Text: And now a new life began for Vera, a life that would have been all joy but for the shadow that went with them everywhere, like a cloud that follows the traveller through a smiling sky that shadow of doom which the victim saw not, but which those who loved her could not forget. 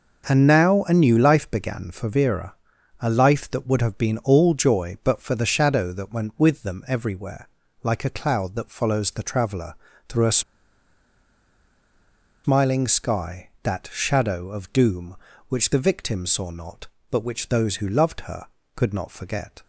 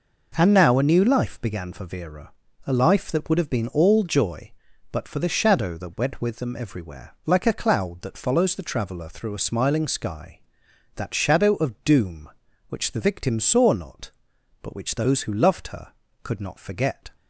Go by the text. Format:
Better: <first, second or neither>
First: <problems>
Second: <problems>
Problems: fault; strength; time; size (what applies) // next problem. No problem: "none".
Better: second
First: pauses between "traveller" and "through"; slight; at 9.7 s; 0.34 s long // pauses between "a" and "smiling"; strong; at 10.4 s; 2.0 s long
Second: none